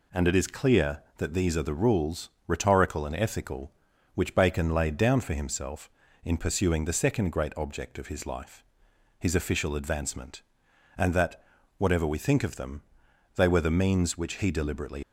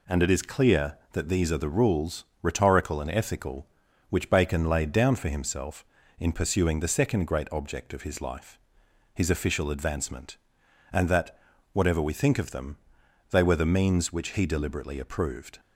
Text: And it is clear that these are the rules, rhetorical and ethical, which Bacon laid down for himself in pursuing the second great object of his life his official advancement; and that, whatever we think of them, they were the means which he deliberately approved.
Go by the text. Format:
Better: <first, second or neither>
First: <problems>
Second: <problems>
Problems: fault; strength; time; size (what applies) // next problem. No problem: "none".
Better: second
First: pauses between "life" and "his"; noticeable; at 8.6 s; 0.58 s long // stops before "approved"; at 15.0 s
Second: pauses between "life" and "his"; noticeable; at 8.5 s; 0.58 s long